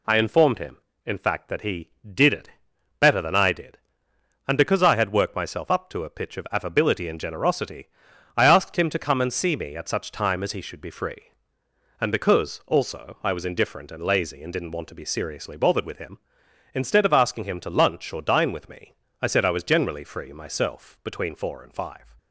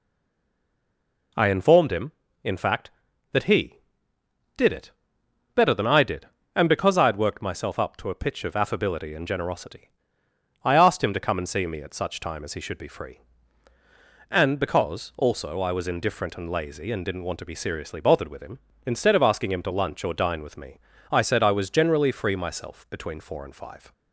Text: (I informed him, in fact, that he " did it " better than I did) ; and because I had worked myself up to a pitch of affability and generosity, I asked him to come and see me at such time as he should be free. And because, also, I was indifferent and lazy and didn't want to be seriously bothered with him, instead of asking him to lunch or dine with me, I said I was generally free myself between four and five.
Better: first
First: none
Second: stays silent before the first word; noticeable; until 1.3 s; 1.3 s long

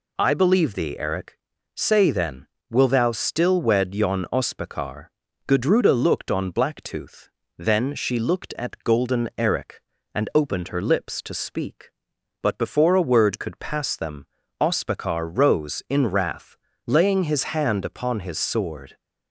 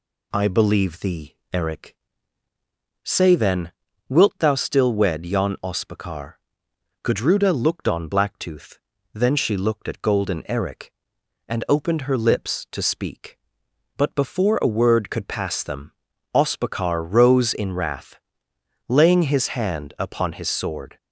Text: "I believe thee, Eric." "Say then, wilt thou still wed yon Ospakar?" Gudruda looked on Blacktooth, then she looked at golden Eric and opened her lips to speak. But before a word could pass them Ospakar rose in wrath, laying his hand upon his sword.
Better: second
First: says "will" for "wilt"; at 2.6 s // pauses between "them" and "Ospakar"; slight; at 14.2 s; 0.34 s long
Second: pauses between "them" and "Ospakar"; at 15.9 s; 0.42 s long

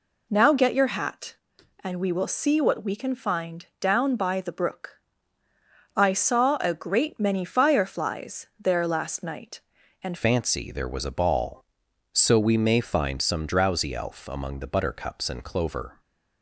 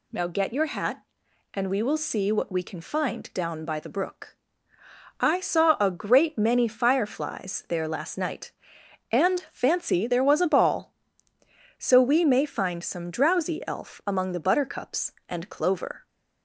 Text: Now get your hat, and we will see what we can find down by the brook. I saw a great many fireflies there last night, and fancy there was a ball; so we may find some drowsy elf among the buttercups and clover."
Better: second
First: changes voice at "fancy"; from 10.1 s on; 5.8 s long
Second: none

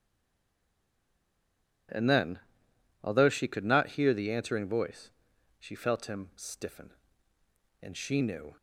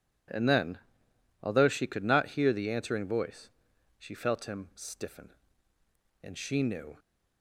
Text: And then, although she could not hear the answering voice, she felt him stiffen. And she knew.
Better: second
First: stays silent before the first word; noticeable; until 1.8 s; 1.8 s long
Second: none

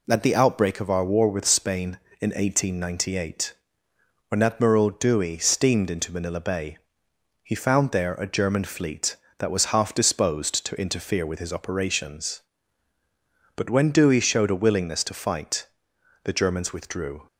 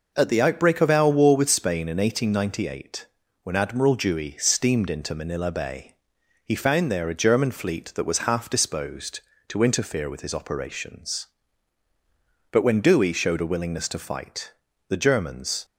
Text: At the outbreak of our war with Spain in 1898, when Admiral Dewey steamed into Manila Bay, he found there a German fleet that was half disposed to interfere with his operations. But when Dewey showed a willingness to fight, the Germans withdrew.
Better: first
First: none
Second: stops before "withdrew"; at 15.6 s

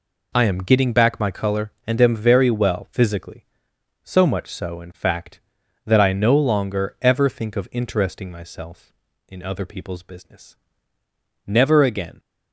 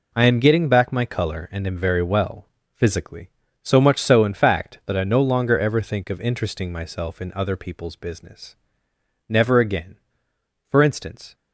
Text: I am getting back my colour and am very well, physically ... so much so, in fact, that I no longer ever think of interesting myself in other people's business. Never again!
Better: first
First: none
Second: goes on to say "For instance"; noticeable; from 10.7 s on; 0.64 s long

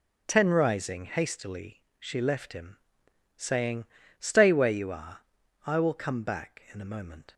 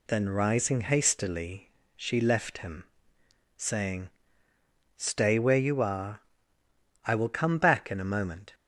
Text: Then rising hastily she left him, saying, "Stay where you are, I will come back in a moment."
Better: second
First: says "Ten" for "Then"; at 0.2 s // pauses between "hastily" and "she"; slight; at 1.8 s; 0.18 s long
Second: pauses between "hastily" and "she"; slight; at 1.7 s; 0.26 s long

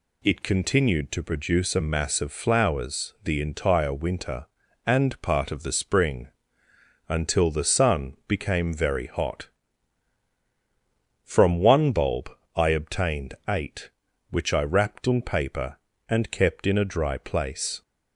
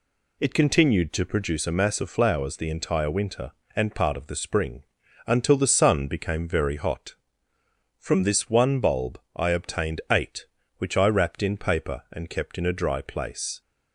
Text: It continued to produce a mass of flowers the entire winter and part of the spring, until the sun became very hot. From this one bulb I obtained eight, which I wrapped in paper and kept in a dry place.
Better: second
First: skips "this"; at 11.5 s // pauses between "bulb" and "I"; slight; at 12.2 s; 0.26 s long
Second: pauses between "bulb" and "I"; slight; at 9.1 s; 0.16 s long

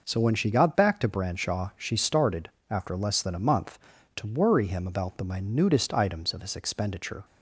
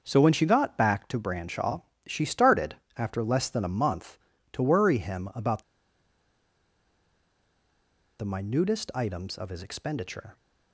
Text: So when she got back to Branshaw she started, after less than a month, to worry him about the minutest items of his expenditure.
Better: first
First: none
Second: starts louder than the rest; until 1.0 s; 6.5 dB // pauses between "Branshaw" and "she"; slight; at 1.8 s; 0.24 s long // pauses between "about" and "the"; strong; at 5.6 s; 2.5 s long

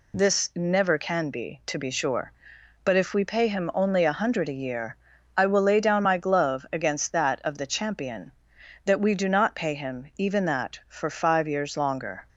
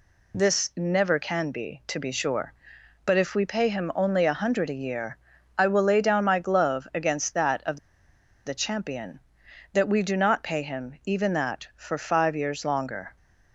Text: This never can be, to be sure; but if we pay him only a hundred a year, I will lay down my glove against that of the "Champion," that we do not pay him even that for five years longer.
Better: first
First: none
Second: pauses between "of" and "the"; noticeable; at 7.7 s; 0.66 s long

